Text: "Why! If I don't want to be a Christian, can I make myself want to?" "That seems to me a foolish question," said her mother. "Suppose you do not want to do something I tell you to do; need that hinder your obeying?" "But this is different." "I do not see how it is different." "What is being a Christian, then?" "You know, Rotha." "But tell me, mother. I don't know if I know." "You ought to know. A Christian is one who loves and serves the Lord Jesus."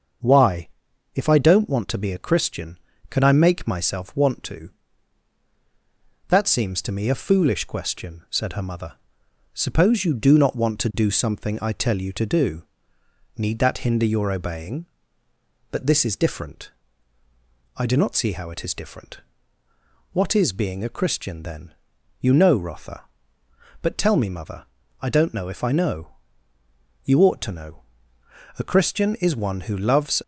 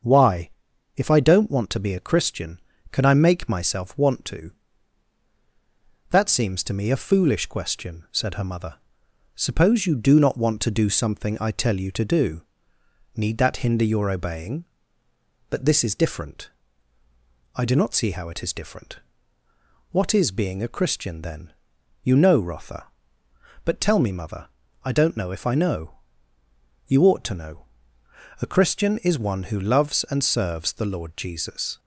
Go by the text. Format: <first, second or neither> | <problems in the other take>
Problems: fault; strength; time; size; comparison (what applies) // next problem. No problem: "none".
second | starts louder than the rest; until 1.7 s; 6.5 dB; also in the second // stops before "and serves the Lord Jesus"; at 30.2 s